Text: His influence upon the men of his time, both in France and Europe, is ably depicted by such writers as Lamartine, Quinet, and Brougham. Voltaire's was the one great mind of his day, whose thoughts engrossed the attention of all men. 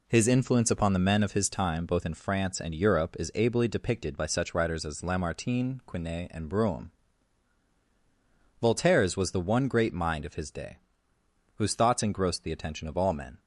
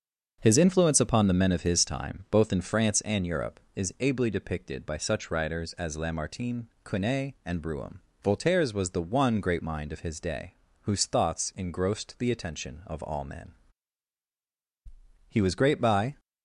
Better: first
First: none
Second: starts louder than the rest; until 1.4 s; 6.5 dB // goes on to say "He was great by"; noticeable; from 15.2 s on; 0.90 s long

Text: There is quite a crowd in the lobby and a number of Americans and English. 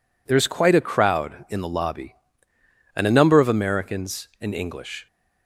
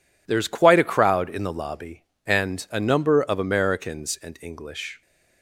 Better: neither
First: none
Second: none

